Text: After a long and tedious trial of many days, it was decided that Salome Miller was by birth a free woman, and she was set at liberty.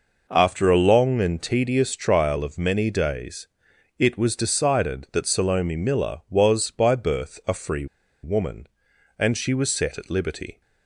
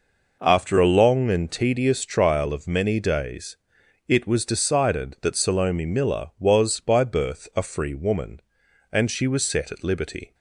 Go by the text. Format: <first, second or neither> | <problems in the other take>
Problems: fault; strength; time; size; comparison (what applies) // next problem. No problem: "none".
second | pauses between "free" and "woman"; at 7.8 s; 0.37 s long